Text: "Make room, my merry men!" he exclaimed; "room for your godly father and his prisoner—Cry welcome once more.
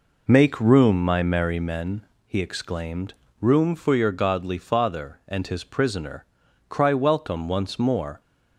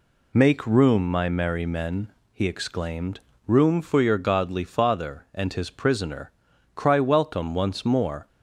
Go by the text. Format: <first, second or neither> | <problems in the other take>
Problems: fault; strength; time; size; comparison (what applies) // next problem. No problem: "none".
second | starts louder than the rest; noticeable; until 1.7 s; 4.5 dB